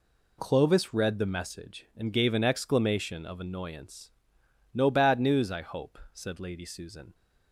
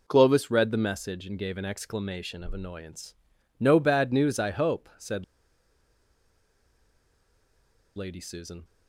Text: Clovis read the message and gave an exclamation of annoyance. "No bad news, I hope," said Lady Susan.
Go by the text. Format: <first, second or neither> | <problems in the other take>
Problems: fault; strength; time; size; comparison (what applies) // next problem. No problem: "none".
first | pauses between "said" and "Lady"; strong; at 5.2 s; 2.7 s long